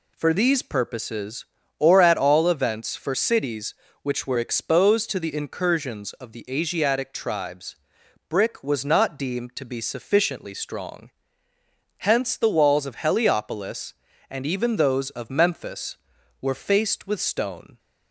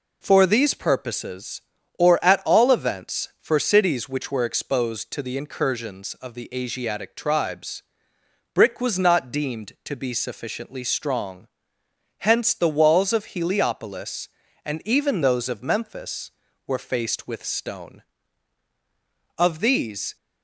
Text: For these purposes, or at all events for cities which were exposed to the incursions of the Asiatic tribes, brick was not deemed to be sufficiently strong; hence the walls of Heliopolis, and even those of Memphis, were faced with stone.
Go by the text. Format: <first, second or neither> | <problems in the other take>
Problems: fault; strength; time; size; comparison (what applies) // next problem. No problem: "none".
first | goes on to say "Of these"; noticeable; from 19.3 s on; 0.78 s long